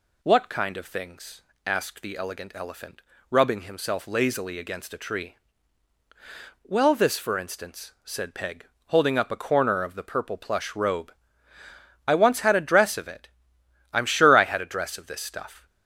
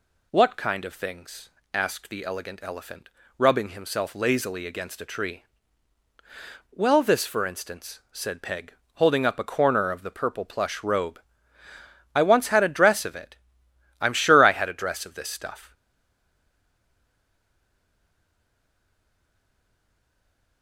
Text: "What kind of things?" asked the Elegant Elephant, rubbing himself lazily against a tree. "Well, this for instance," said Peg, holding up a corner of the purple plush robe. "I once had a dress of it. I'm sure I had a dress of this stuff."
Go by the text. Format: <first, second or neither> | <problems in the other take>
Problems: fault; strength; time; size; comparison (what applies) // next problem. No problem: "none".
first | stays silent after the last word; strong; from 15.7 s on; 4.9 s long